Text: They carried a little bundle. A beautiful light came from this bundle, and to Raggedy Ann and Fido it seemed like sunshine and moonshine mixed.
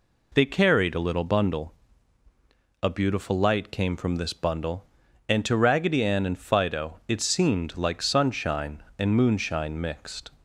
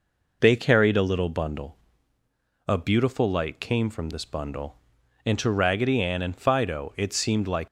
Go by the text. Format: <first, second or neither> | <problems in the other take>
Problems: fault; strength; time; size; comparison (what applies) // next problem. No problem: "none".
first | stops before "sunshine and moonshine mixed"; at 7.6 s